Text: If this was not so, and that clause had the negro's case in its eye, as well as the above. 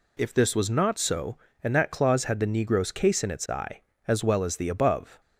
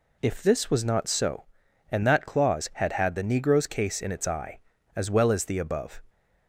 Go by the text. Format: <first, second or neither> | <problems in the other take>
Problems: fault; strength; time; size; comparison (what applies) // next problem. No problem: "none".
first | says "had" twice; at 2.9 s